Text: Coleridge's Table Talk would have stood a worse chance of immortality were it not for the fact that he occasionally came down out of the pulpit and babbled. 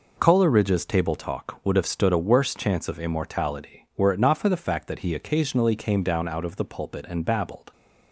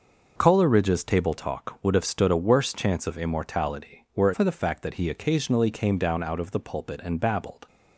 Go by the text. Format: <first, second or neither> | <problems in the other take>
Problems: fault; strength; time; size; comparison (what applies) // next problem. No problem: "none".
first | skips "not"; at 4.3 s